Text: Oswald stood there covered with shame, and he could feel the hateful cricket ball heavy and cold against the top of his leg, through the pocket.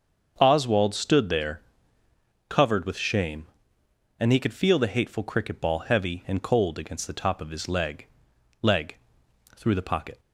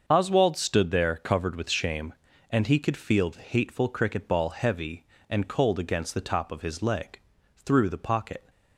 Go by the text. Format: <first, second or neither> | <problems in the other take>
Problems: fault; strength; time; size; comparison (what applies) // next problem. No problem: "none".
second | starts louder than the rest; until 1.3 s; 6.5 dB; also in the second // pauses between "there" and "covered"; noticeable; at 1.6 s; 0.88 s long // says "leg" twice; at 8.6 s